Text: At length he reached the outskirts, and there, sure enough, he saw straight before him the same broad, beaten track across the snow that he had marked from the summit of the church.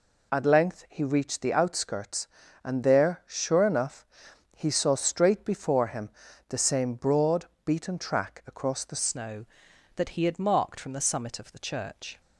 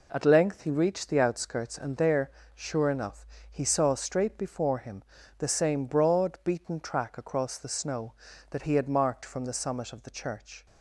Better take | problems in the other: second | pauses between "him" and "the"; at 6.0 s; 0.38 s long; slight in the second // changes voice at "snow"; from 8.9 s on; 3.2 s long

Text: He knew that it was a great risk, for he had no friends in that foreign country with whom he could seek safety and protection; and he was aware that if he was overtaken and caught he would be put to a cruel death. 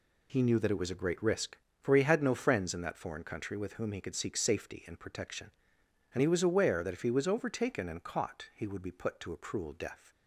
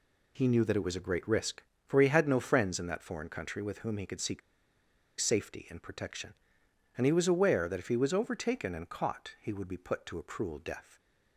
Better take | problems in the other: first | pauses between "seek" and "safety"; noticeable; at 4.4 s; 0.79 s long

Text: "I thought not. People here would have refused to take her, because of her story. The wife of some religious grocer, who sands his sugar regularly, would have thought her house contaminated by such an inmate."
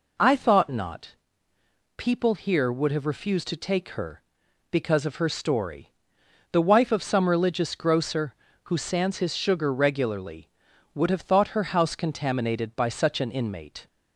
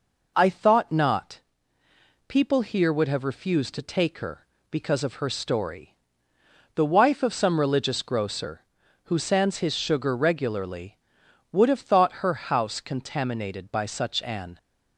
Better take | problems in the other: first | stops before "inmate"; at 14.5 s

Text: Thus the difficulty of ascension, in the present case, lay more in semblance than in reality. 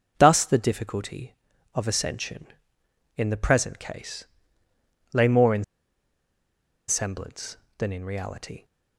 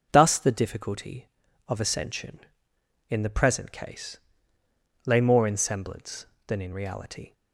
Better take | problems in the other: second | pauses between "in" and "semblance"; at 5.6 s; 1.2 s long

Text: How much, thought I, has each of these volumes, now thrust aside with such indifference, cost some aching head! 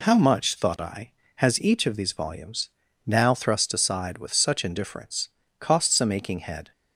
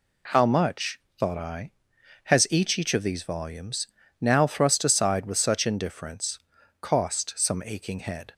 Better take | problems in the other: first | says "each" twice; at 2.7 s

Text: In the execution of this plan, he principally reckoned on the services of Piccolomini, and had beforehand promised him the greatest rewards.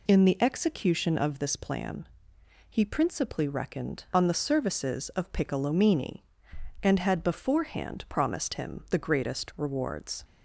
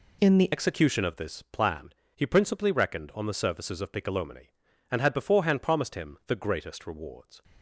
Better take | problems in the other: first | changes voice at "execution"; from 0.5 s on; 6.9 s long

